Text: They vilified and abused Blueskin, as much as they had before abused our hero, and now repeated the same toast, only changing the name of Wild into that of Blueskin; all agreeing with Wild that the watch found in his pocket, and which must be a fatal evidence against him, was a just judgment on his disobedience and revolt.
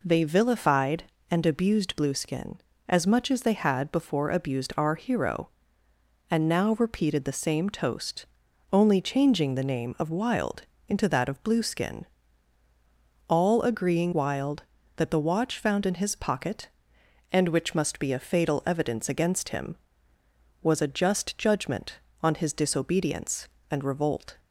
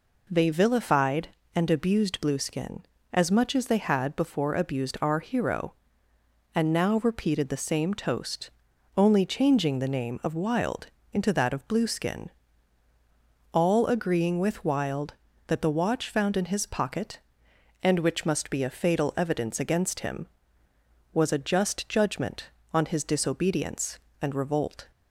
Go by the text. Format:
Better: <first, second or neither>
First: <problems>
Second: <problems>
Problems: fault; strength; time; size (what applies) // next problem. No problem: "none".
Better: second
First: pauses between "Wild" and "into"; slight; at 10.6 s; 0.26 s long // skips "with"; at 14.1 s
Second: pauses between "Wild" and "into"; slight; at 10.8 s; 0.26 s long